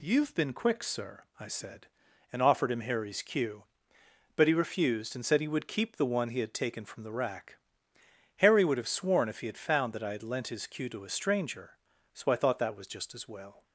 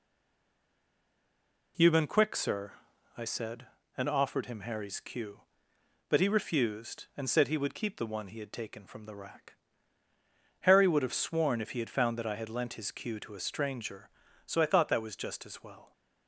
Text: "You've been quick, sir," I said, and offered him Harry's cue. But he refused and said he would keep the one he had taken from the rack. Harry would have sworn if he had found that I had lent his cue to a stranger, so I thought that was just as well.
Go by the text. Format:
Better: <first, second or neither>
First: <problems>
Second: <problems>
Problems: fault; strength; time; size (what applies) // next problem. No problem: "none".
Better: first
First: none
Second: stays silent before the first word; noticeable; until 1.7 s; 1.7 s long